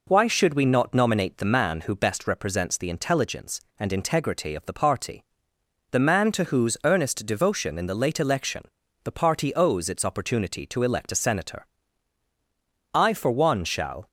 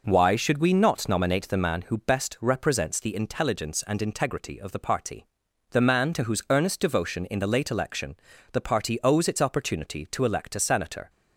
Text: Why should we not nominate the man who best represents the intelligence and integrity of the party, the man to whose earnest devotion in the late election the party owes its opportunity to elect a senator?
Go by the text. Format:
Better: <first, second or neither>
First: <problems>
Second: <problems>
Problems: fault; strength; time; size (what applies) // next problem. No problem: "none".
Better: second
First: pauses between "election" and "the"; at 8.6 s; 0.40 s long // goes on to say "I for one shall"; noticeable; from 12.9 s on; 1.1 s long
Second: pauses between "election" and "the"; slight; at 8.1 s; 0.36 s long